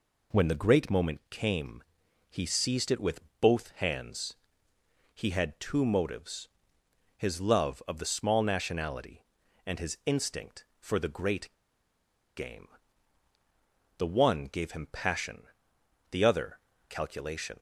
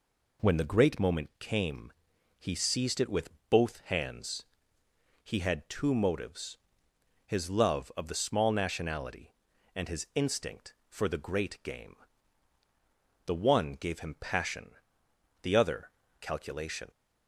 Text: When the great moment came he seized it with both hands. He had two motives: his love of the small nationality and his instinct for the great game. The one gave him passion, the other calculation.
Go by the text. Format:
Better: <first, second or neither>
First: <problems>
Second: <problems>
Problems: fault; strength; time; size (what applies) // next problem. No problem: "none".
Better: second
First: pauses between "came" and "he"; noticeable; at 1.8 s; 0.46 s long // pauses between "with" and "both"; slight; at 3.1 s; 0.22 s long // pauses between "great" and "game"; noticeable; at 11.5 s; 0.82 s long // pauses between "other" and "calculation"; slight; at 16.5 s; 0.30 s long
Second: pauses between "came" and "he"; noticeable; at 1.9 s; 0.46 s long // pauses between "with" and "both"; slight; at 3.2 s; 0.22 s long // pauses between "other" and "calculation"; slight; at 15.9 s; 0.30 s long